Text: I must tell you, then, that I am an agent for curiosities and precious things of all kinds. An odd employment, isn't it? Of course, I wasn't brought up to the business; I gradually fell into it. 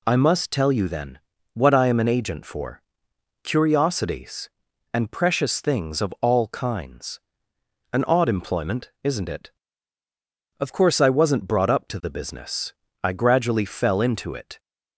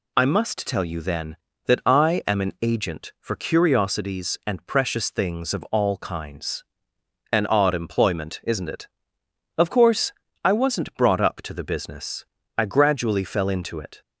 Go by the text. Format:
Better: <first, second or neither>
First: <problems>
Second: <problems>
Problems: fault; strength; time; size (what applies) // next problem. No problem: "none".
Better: second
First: says "what" for "that"; at 1.5 s // pauses between "for" and "curiosities"; noticeable; at 2.8 s; 0.62 s long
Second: none